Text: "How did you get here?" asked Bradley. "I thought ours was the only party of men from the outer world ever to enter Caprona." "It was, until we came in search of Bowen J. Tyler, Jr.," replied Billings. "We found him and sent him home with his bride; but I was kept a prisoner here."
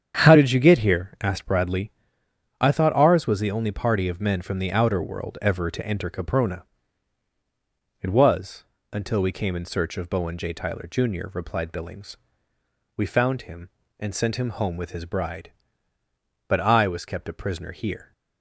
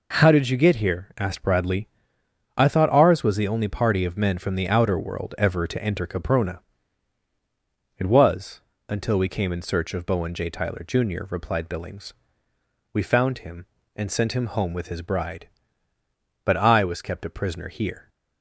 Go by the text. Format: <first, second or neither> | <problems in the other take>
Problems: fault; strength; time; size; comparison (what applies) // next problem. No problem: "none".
second | starts louder than the rest; strong; until 1.4 s; 8.5 dB